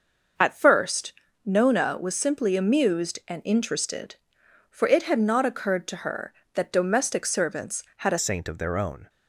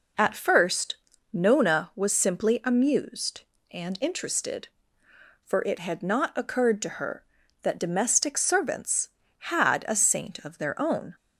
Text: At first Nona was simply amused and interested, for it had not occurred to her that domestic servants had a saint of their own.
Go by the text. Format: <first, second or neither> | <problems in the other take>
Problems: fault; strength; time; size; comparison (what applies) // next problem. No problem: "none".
second | starts louder than the rest; noticeable; until 1.7 s; 6 dB // pauses between "first" and "Nona"; slight; at 1.1 s; 0.32 s long; also in the second // changes voice at "saint"; from 8.1 s on; 0.9 s long